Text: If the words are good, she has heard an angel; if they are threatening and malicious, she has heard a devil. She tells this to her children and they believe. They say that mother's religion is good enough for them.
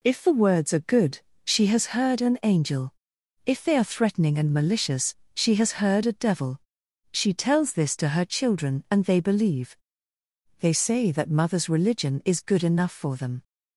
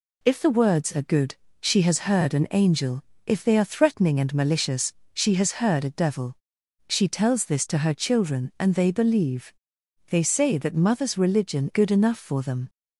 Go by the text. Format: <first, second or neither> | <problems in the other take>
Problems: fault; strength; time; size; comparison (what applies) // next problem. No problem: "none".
first | skips "is"; at 11.7 s